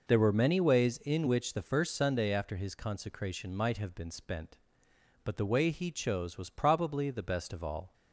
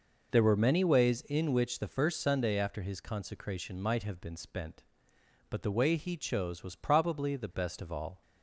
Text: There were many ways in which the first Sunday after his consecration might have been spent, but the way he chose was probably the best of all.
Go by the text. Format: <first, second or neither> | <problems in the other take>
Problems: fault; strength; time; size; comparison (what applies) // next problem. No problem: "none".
neither | none